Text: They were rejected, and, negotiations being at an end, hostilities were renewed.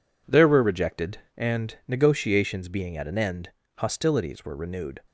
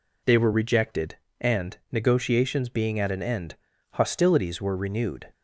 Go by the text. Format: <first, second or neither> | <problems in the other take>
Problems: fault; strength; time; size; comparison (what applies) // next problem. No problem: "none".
second | says "There" for "They"; at 0.2 s